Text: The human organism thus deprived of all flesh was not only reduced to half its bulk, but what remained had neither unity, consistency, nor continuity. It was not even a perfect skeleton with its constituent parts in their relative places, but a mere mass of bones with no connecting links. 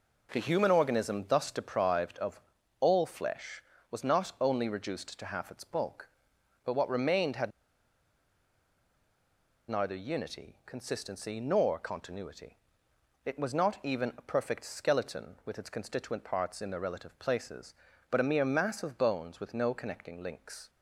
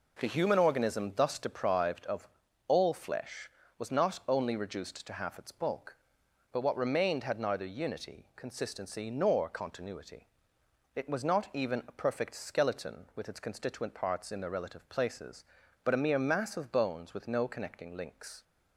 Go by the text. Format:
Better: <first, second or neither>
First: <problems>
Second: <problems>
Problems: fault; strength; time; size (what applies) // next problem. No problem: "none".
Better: second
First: pauses between "of" and "all"; at 2.3 s; 0.40 s long // pauses between "had" and "neither"; strong; at 7.4 s; 2.1 s long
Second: pauses between "of" and "all"; at 2.2 s; 0.40 s long